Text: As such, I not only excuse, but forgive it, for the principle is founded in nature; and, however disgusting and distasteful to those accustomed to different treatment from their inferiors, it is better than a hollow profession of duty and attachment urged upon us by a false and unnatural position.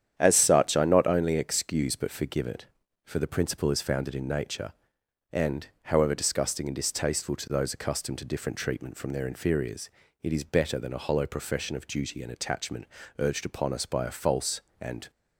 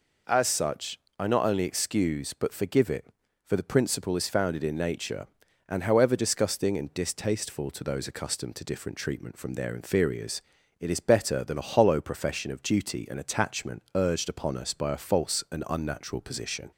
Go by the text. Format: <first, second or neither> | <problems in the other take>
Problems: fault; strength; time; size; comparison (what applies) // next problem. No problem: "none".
second | starts louder than the rest; strong; until 1.1 s; 9.5 dB // pauses between "attachment" and "urged"; slight; at 12.8 s; 0.32 s long // stops before "unnatural position"; at 15.0 s